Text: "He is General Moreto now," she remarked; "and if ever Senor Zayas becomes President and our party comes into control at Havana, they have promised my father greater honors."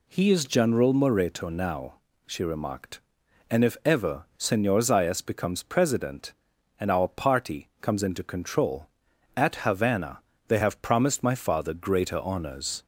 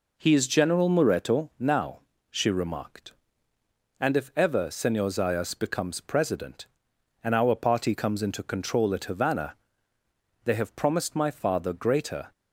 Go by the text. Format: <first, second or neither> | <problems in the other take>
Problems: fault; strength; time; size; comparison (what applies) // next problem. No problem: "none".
first | stops before "honors"; at 12.3 s